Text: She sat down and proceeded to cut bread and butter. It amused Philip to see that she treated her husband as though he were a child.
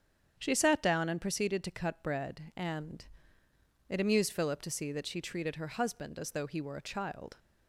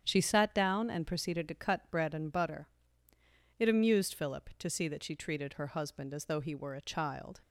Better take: second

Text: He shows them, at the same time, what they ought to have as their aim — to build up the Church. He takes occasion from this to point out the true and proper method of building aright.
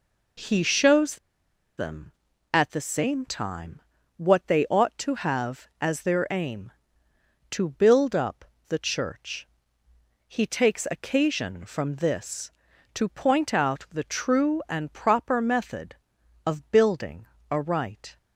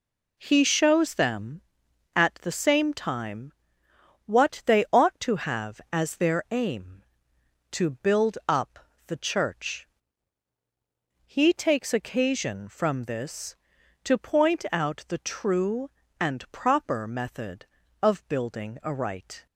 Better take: second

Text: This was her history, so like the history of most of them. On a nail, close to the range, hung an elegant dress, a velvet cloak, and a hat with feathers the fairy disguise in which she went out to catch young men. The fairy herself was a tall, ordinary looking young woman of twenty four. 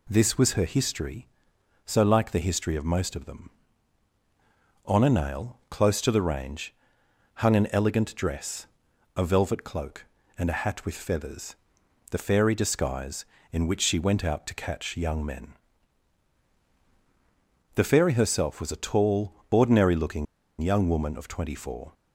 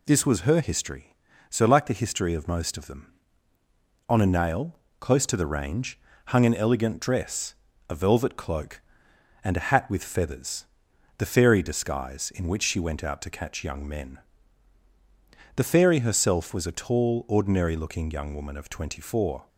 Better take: second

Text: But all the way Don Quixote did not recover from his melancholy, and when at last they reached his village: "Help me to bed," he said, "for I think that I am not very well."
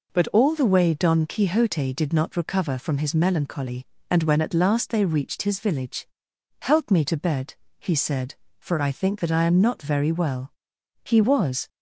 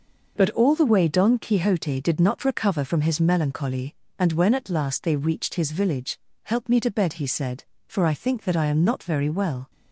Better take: second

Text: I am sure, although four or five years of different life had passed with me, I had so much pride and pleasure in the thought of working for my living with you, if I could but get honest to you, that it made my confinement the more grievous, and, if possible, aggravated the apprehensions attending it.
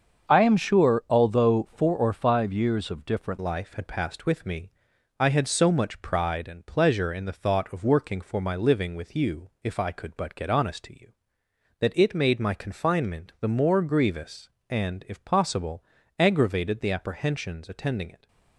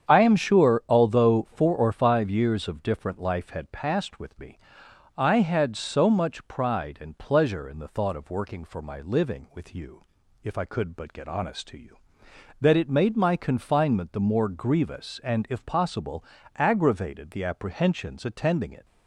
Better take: second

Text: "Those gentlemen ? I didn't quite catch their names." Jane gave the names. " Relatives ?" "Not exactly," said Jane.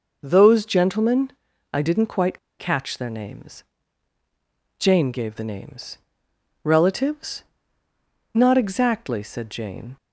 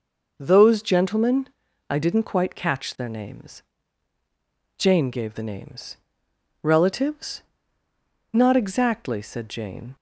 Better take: second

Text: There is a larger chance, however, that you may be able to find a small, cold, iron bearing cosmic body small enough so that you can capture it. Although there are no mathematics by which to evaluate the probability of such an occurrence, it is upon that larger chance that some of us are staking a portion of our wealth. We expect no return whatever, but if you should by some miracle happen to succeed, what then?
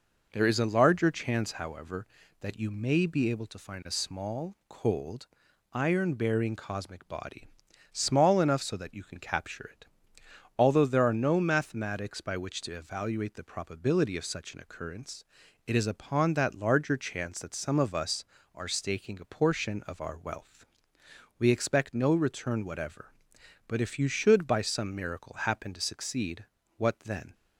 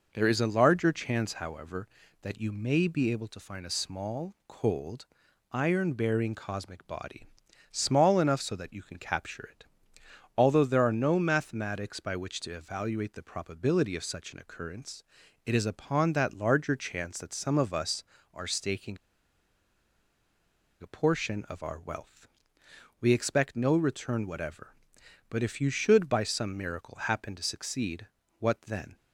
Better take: first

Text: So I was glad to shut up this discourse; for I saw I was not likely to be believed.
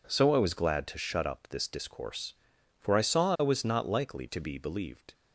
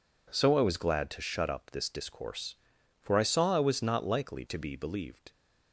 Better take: neither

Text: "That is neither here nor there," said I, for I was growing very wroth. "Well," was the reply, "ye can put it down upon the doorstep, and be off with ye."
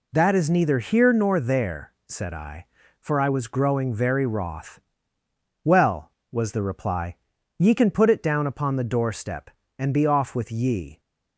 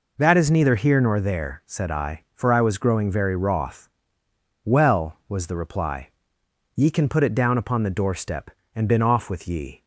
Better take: first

